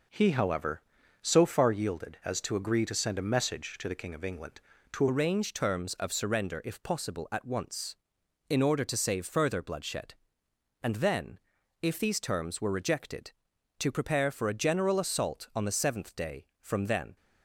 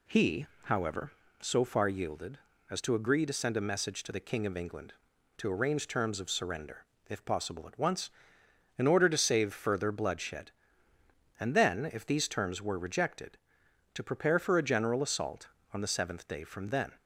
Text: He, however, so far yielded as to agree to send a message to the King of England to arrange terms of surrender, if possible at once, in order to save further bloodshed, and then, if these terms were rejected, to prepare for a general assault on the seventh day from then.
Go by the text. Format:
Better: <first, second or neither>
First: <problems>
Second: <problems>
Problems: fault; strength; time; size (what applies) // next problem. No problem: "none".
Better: second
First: changes voice at "arrange"; from 5.0 s on; 12.1 s long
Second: none